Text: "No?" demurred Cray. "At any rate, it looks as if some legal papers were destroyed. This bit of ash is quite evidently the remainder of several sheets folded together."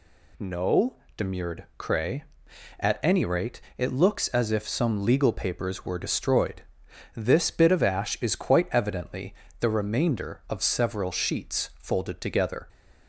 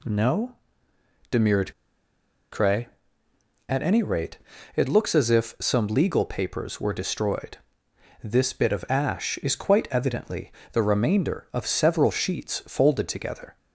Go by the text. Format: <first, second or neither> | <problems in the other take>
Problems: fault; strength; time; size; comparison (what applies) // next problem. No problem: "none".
first | pauses between "demurred" and "Cray"; noticeable; at 1.7 s; 0.80 s long // pauses between "evidently" and "the"; slight; at 10.5 s; 0.22 s long; slight in the first